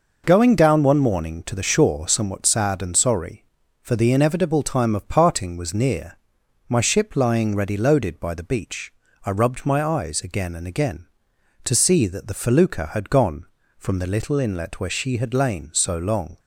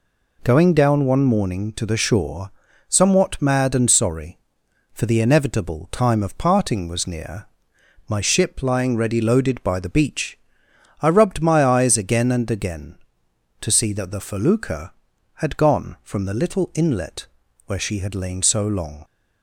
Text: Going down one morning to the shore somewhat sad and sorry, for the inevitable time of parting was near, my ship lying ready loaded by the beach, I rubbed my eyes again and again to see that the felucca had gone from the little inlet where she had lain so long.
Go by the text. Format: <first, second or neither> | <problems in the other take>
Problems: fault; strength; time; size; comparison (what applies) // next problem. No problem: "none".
first | pauses between "shore" and "somewhat"; at 2.5 s; 0.38 s long // says "mad" for "sad"; at 3.4 s // pauses between "inlet" and "where"; at 17.2 s; 0.40 s long